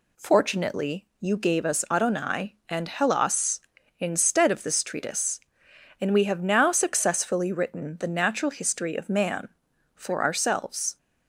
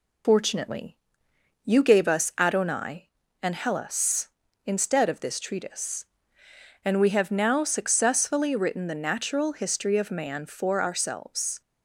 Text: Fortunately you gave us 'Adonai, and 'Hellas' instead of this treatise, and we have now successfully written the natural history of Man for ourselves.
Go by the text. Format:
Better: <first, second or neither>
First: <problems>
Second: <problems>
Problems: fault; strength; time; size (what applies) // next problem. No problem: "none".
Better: first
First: none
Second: loses the start of "Fortunately"; at 0.2 s; 120 ms // pauses between "Fortunately" and "you"; noticeable; at 0.9 s; 0.66 s long